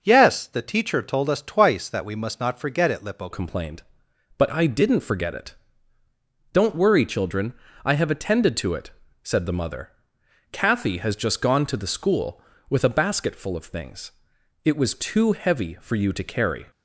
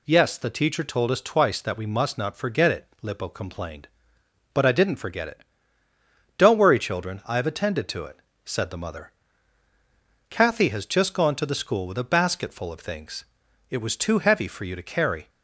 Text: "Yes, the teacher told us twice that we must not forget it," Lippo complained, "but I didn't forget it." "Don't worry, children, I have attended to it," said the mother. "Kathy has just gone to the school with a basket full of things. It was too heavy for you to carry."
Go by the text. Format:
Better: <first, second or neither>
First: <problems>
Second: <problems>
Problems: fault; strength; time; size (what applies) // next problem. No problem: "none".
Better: second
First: changes voice at "complained"; from 3.3 s on; 13.3 s long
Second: none